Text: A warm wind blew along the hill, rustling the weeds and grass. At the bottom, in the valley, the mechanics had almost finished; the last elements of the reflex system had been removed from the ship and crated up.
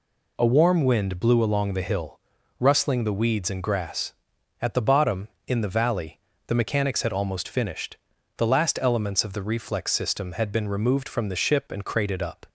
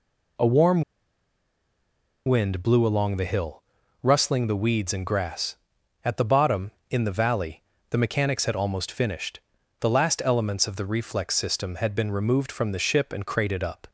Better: first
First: none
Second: pauses between "warm" and "wind"; strong; at 0.8 s; 1.4 s long

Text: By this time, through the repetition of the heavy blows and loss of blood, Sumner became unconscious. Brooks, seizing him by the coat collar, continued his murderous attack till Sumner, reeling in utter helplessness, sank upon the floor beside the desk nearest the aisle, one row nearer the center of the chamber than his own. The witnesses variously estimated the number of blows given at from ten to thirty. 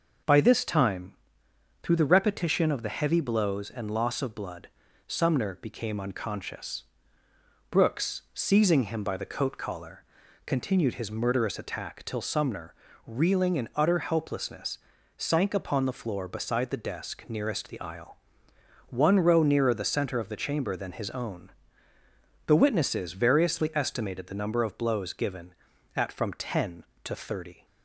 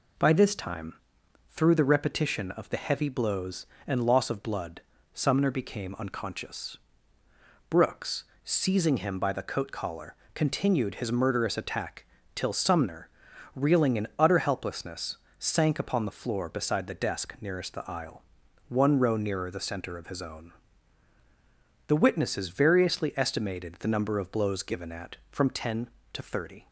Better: first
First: none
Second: pauses between "attack" and "till"; slight; at 12.0 s; 0.28 s long // skips "the chamber than"; at 20.0 s

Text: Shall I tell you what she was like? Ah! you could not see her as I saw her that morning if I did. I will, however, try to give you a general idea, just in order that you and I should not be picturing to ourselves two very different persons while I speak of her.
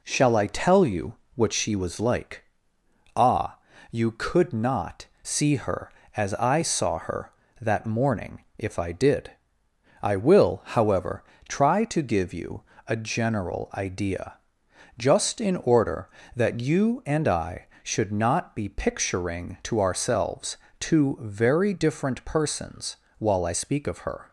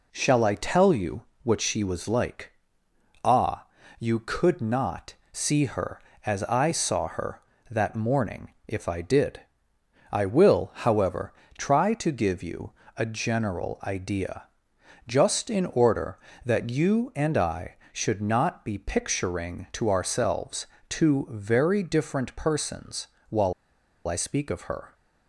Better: first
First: pauses between "you" and "what"; slight; at 1.1 s; 0.20 s long // pauses between "not" and "see"; slight; at 5.0 s; 0.17 s long // pauses between "morning" and "if"; slight; at 8.4 s; 0.16 s long // pauses between "you" and "a"; slight; at 12.6 s; 0.26 s long // pauses between "ourselves" and "two"; slight; at 20.5 s; 0.24 s long // pauses between "persons" and "while"; slight; at 22.9 s; 0.22 s long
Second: pauses between "you" and "what"; slight; at 1.2 s; 0.20 s long // pauses between "not" and "see"; slight; at 5.1 s; 0.18 s long // pauses between "morning" and "if"; slight; at 8.5 s; 0.16 s long // pauses between "you" and "a"; slight; at 12.7 s; 0.26 s long // pauses between "ourselves" and "two"; slight; at 20.6 s; 0.24 s long // pauses between "persons" and "while"; slight; at 23.0 s; 0.22 s long // pauses between "while" and "I"; noticeable; at 23.5 s; 0.54 s long

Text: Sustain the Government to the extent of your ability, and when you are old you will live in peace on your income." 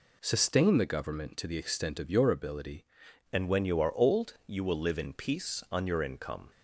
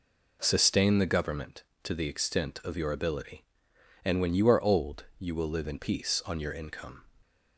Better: second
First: changes voice at "and"; from 3.3 s on; 3.1 s long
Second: none

